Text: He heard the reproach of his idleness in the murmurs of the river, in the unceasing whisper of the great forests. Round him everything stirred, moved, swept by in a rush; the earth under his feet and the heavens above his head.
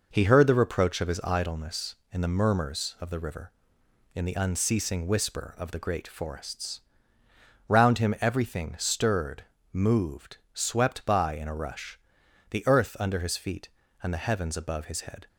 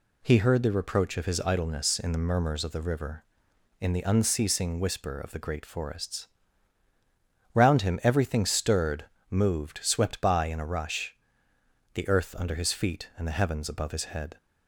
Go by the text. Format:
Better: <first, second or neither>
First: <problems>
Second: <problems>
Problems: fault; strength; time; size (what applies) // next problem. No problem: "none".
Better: neither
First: none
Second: none